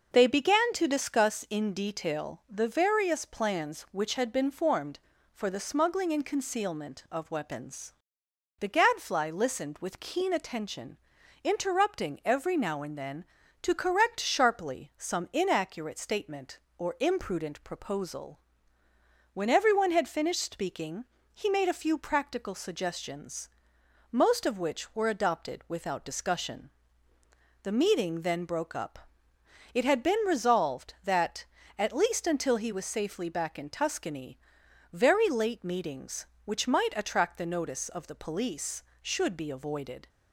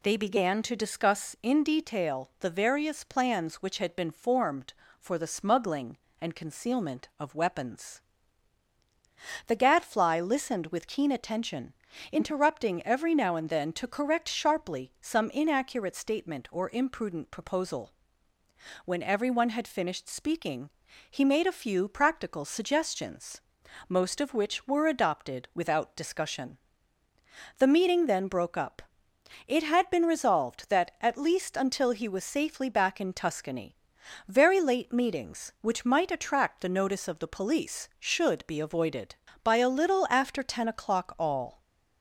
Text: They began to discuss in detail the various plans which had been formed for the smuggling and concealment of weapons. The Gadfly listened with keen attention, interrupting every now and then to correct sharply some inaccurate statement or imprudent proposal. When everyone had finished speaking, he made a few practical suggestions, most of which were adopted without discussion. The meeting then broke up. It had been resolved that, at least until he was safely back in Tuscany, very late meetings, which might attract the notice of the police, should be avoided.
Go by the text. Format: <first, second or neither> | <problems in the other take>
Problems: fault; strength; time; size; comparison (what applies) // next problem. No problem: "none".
first | goes on to say "By a little after ten o'clock all"; strong; from 39.4 s on; 2.1 s long